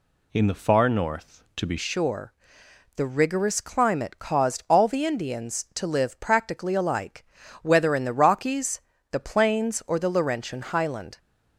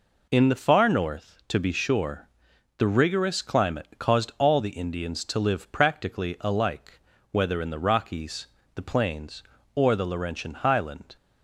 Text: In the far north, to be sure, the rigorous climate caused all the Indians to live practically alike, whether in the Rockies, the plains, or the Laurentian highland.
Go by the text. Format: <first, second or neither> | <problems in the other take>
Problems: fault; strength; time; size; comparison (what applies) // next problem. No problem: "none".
second | changes voice at "sure"; from 1.7 s on; 9.4 s long